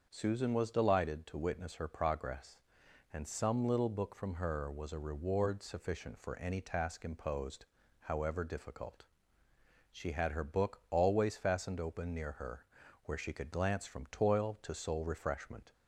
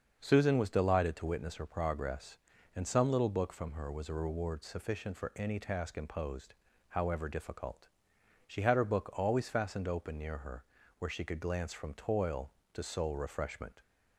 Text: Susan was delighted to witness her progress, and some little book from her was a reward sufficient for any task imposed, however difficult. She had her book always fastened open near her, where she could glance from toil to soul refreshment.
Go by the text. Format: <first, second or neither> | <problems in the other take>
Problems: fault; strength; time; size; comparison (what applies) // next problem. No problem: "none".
neither | starts louder than the rest; the same in both